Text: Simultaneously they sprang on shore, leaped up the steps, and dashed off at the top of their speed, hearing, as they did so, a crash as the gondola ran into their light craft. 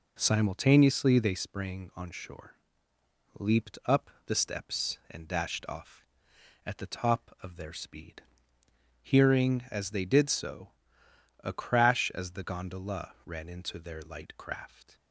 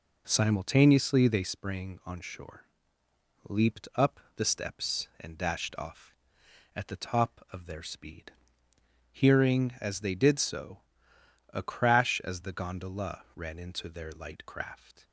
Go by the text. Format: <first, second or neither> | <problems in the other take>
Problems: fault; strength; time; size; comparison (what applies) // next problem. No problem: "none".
neither | pauses between "up" and "the"; slight; the same in both